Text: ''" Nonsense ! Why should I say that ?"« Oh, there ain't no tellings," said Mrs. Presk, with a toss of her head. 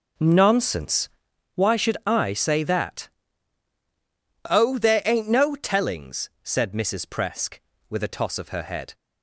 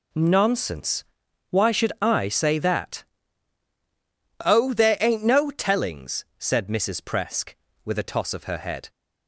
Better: second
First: starts louder than the rest; slight; until 1.5 s; 3 dB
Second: none

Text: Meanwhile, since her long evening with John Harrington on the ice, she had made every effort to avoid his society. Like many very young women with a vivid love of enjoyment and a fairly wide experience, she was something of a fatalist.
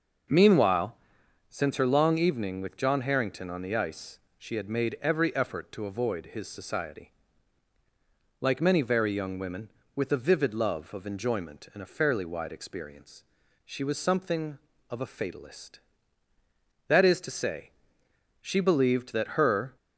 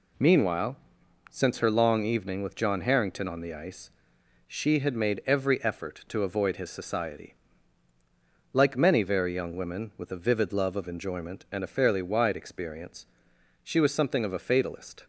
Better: second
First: starts louder than the rest; noticeable; until 1.8 s; 6 dB // goes on to say "That is to say she believed that her"; strong; from 16.8 s on; 2.8 s long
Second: none

